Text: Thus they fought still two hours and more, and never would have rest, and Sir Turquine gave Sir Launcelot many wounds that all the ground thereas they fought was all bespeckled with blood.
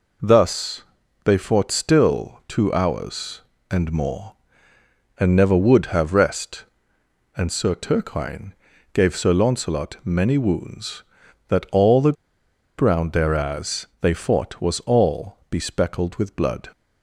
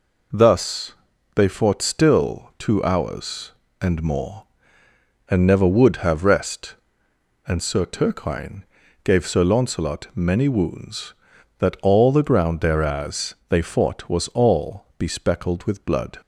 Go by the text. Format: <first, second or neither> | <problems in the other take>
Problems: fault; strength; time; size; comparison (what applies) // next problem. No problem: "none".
second | pauses between "Thus" and "they"; at 0.8 s; 0.42 s long; also in the second // pauses between "Turquine" and "gave"; at 8.5 s; 0.40 s long; also in the second // pauses between "the" and "ground"; noticeable; at 12.1 s; 0.65 s long